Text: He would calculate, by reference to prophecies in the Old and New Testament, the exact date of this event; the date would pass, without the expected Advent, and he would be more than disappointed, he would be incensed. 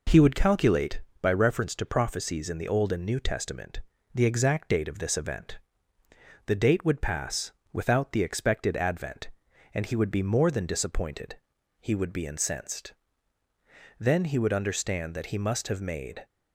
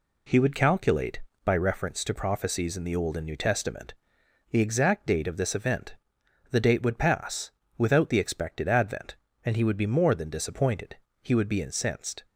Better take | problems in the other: second | goes on to say "Then he would understand that he must have made"; strong; from 13.9 s on; 2.2 s long

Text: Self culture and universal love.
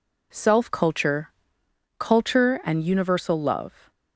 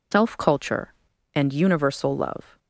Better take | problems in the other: second | says "culture" twice; at 1.9 s

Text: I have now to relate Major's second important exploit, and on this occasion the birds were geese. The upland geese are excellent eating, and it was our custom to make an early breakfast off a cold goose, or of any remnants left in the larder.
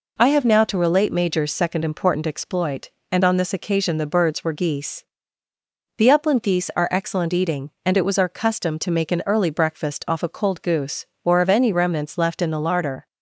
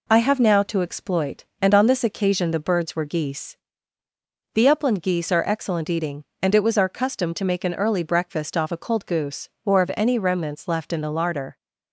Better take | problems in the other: first | skips "relate Major's second important"; at 0.8 s

